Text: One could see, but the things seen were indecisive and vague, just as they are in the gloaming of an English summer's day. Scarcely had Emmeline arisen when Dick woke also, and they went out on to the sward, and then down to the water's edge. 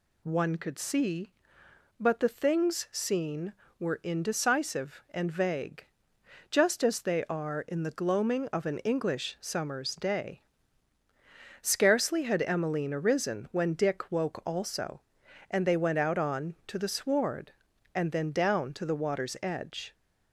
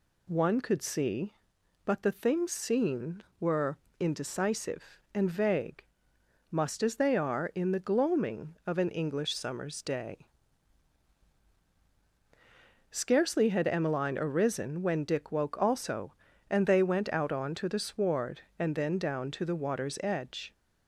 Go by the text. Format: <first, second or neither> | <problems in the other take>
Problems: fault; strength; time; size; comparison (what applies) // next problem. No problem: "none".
first | pauses between "were" and "indecisive"; slight; at 3.7 s; 0.20 s long // says "must" for "just"; at 6.5 s